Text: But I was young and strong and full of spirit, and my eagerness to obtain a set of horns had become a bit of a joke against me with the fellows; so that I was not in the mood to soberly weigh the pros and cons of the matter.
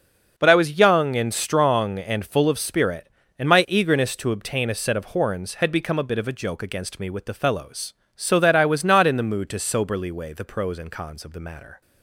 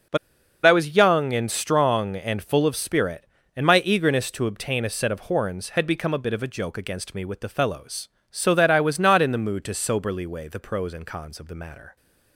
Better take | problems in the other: first | pauses between "But" and "I"; noticeable; at 0.1 s; 0.50 s long

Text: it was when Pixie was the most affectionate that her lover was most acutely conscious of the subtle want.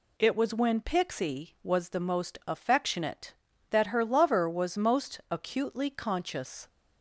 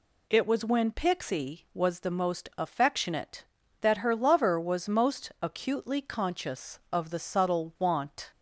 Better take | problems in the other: second | stops before "of the subtle want"; at 6.6 s

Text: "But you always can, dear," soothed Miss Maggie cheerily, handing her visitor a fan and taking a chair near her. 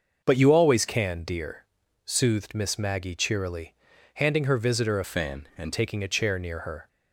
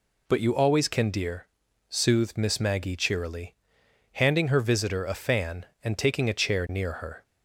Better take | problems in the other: second | starts louder than the rest; until 1.2 s; 6.5 dB // changes voice from "fan" to "and"; from 5.0 to 5.7 s; 0.7 s long

